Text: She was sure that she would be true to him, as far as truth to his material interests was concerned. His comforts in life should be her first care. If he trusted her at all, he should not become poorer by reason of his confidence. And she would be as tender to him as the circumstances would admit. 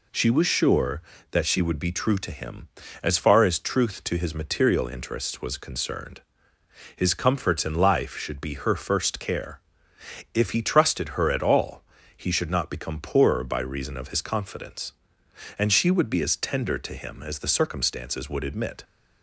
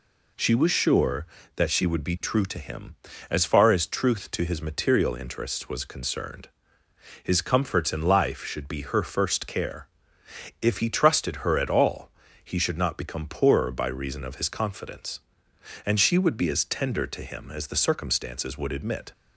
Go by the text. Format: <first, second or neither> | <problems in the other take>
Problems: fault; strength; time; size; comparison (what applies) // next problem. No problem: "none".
neither | none